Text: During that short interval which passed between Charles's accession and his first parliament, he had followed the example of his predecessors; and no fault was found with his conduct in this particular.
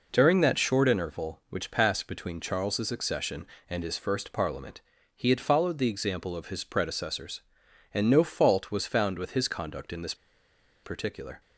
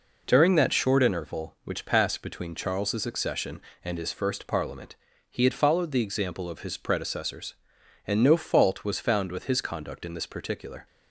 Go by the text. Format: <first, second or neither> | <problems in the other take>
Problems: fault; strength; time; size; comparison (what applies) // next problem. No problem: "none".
second | pauses between "this" and "particular"; noticeable; at 10.1 s; 0.68 s long